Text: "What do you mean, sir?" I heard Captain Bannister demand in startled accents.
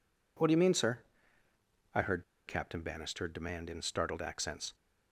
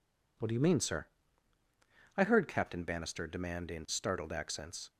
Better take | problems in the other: second | pauses between "heard" and "Captain"; slight; at 2.2 s; 0.23 s long

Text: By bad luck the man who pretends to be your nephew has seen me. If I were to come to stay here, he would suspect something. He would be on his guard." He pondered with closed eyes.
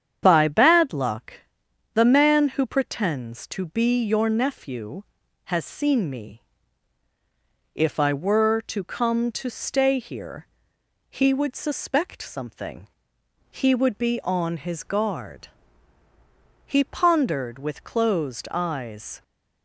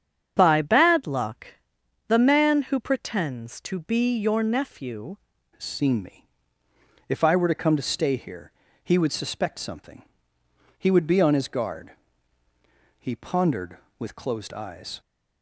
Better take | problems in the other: first | starts louder than the rest; strong; until 1.3 s; 8 dB; strong in the first // pauses between "luck" and "the"; noticeable; at 1.4 s; 0.58 s long; noticeable in the first // changes voice at "has"; from 5.5 s on; 9.5 s long

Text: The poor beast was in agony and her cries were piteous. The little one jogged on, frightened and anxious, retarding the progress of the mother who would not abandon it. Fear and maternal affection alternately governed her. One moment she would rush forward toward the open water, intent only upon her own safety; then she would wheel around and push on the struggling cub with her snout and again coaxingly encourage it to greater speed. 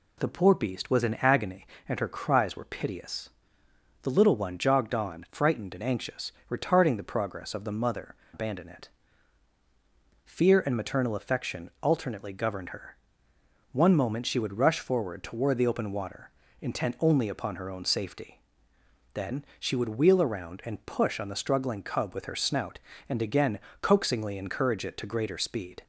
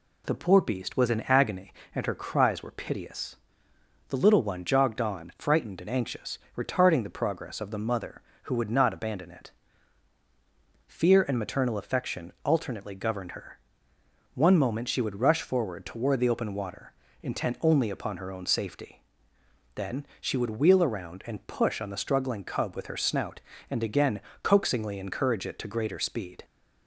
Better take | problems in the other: second | skips "who would not"; at 8.2 s // pauses between "again" and "coaxingly"; slight; at 23.5 s; 0.22 s long; slight in the second

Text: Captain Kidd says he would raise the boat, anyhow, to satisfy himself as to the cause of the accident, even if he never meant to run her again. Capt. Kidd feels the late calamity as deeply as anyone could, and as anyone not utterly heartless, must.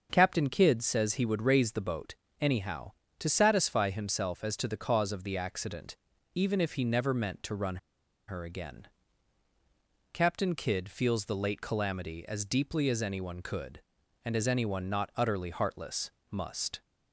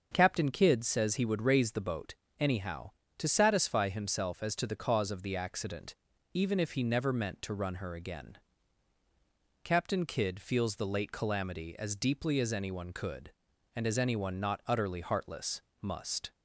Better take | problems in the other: second | starts louder than the rest; until 1.1 s; 6.5 dB; also in the second // pauses between "run" and "her"; noticeable; at 7.7 s; 0.51 s long

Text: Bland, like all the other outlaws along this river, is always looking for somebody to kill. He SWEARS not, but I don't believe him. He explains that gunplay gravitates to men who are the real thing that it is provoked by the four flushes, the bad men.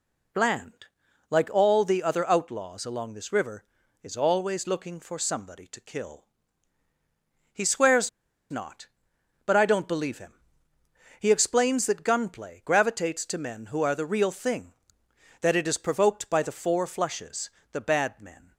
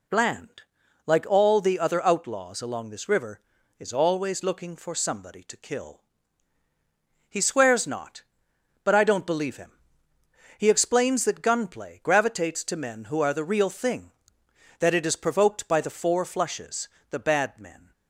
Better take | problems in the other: second | pauses between "SWEARS" and "not"; at 8.0 s; 0.41 s long

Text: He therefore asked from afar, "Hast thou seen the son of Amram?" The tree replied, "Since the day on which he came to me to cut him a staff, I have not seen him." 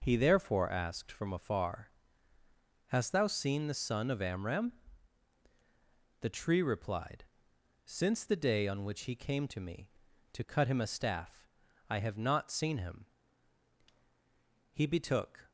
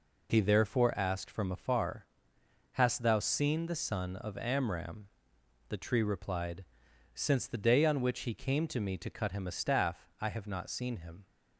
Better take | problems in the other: second | goes on to say "He betook"; noticeable; from 14.7 s on; 0.78 s long

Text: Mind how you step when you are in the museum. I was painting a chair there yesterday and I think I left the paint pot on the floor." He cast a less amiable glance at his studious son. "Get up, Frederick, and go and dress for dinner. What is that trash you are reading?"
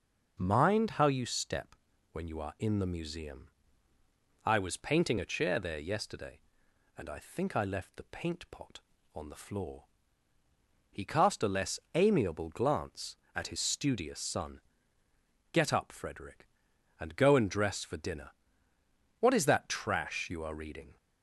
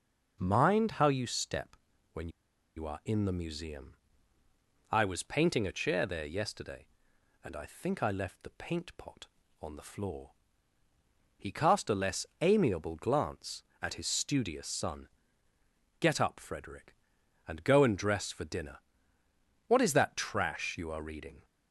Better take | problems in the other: first | pauses between "step" and "when"; at 1.7 s; 0.38 s long; also in the first // pauses between "when" and "you"; noticeable; at 2.2 s; 0.47 s long // pauses between "less" and "amiable"; slight; at 12.2 s; 0.18 s long; slight in the first

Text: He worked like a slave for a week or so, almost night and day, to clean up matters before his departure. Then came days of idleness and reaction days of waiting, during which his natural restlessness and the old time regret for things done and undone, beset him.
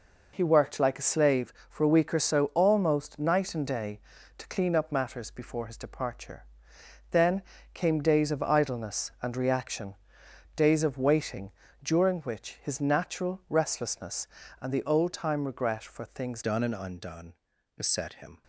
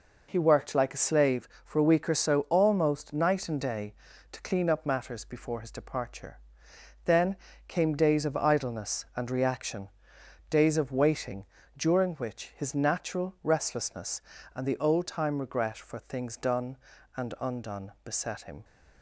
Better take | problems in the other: second | pauses between "Then" and "came"; slight; at 7.4 s; 0.30 s long; slight in the second // pauses between "reaction" and "days"; noticeable; at 9.9 s; 0.62 s long; noticeable in the second // changes voice at "done"; from 16.4 s on; 2.0 s long

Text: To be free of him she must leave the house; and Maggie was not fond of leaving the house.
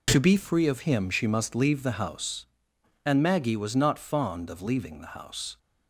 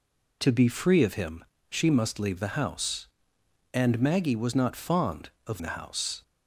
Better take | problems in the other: first | pauses between "him" and "she"; slight; at 1.4 s; 0.26 s long // skips "leaving"; at 5.6 s

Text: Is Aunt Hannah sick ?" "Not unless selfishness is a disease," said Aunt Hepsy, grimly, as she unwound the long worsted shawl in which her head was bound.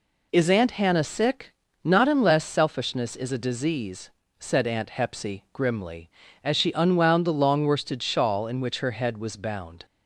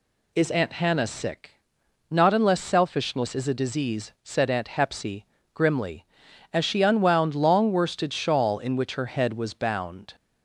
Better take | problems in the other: first | skips "the"; at 7.3 s

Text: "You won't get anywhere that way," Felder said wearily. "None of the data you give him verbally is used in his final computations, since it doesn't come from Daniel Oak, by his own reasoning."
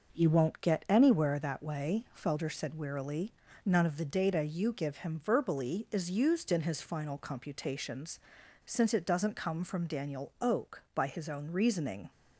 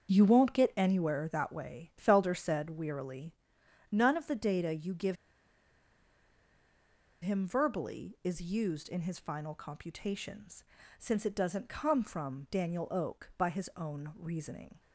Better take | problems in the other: first | starts louder than the rest; until 1.1 s; 7 dB // pauses between "give" and "him"; strong; at 5.1 s; 2.0 s long

